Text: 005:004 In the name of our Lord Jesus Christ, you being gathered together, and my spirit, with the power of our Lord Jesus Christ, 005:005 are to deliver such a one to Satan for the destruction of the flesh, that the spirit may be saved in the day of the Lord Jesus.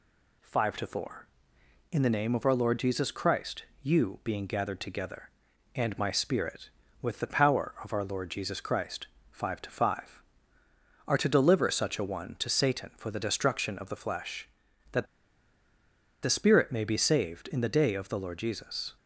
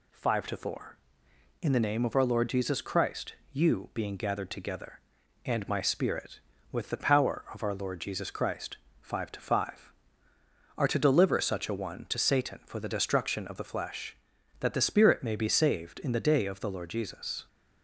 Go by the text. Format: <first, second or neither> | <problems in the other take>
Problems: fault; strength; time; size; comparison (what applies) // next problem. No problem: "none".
second | pauses between "that" and "the"; at 15.0 s; 1.1 s long